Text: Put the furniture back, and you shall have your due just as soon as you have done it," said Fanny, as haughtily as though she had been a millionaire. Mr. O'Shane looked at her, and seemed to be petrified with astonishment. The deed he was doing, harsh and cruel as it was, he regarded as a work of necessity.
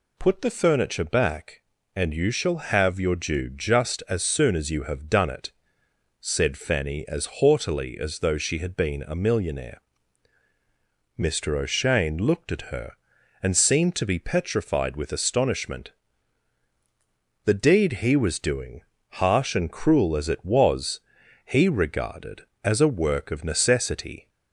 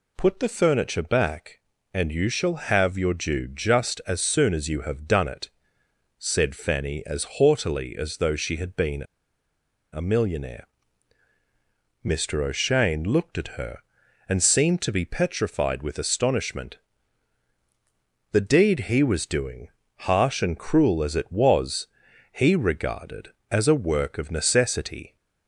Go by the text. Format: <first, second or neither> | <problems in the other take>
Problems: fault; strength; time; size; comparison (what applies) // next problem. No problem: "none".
first | pauses between "been" and "a"; noticeable; at 9.0 s; 0.89 s long